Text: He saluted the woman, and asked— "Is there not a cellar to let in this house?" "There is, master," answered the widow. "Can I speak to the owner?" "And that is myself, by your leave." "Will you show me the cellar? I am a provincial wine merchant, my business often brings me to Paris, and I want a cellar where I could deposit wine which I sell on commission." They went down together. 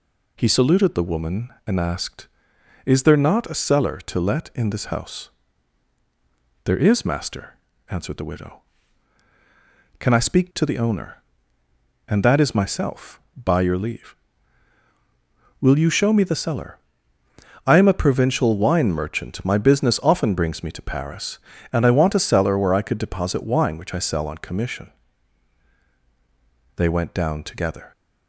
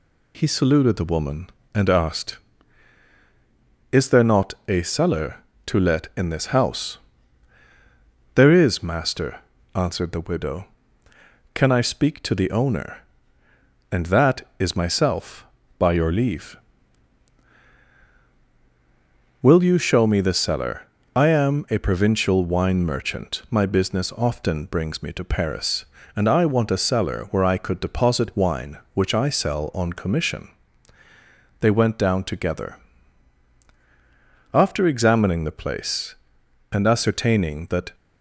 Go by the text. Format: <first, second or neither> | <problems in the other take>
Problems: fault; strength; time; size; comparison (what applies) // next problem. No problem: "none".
first | goes on to say "After examining the place and ascertaining that"; strong; from 34.5 s on; 3.4 s long